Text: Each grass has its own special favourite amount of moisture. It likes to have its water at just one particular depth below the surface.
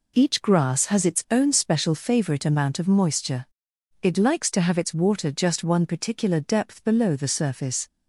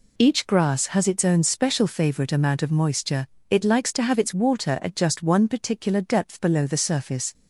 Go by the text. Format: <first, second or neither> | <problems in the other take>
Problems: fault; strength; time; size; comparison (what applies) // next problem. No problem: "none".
second | skips "at"; at 5.3 s